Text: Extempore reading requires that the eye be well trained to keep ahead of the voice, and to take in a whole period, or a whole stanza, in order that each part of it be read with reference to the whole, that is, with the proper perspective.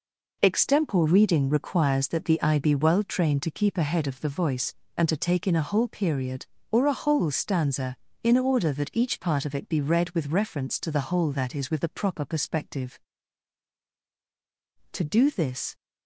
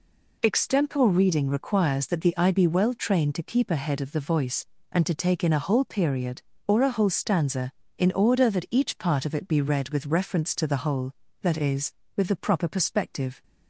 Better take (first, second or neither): second